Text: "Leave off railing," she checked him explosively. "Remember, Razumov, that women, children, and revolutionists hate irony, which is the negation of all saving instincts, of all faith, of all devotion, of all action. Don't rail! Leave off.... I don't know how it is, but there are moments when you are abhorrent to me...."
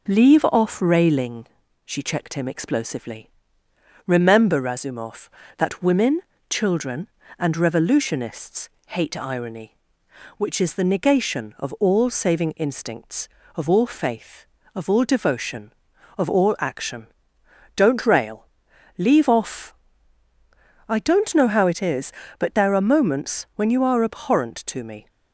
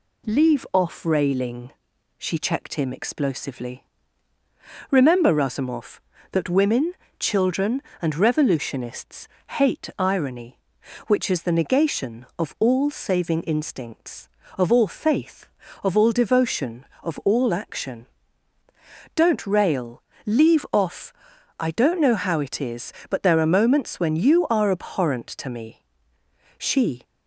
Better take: first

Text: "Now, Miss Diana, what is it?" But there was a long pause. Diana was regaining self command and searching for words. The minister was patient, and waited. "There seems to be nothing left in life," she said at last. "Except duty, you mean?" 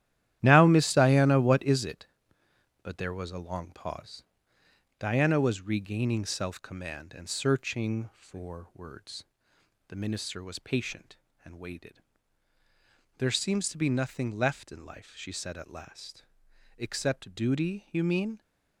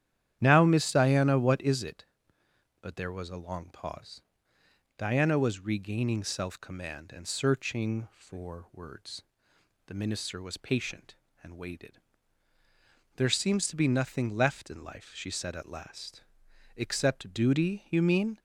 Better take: second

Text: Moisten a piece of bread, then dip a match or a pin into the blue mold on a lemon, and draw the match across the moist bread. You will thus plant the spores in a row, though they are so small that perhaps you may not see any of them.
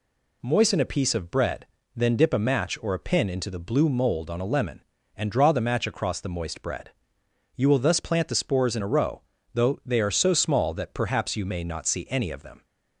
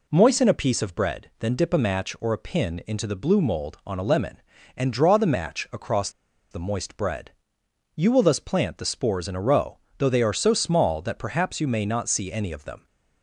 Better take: first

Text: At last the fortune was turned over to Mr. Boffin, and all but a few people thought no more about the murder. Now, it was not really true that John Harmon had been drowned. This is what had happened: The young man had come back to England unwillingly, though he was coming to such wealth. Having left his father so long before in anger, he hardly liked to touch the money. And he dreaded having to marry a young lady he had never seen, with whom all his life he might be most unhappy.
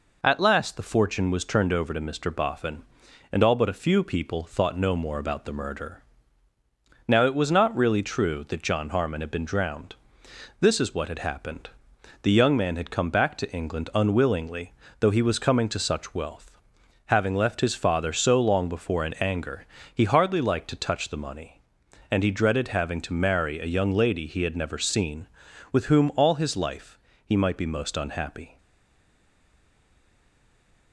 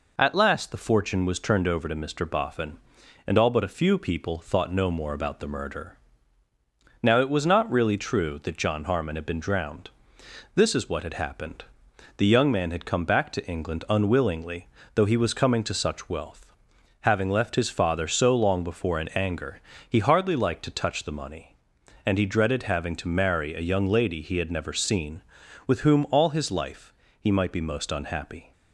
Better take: second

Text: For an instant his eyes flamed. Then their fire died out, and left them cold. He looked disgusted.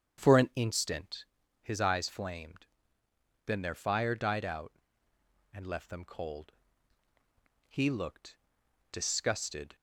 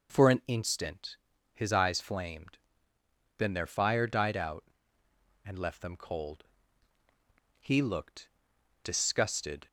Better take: second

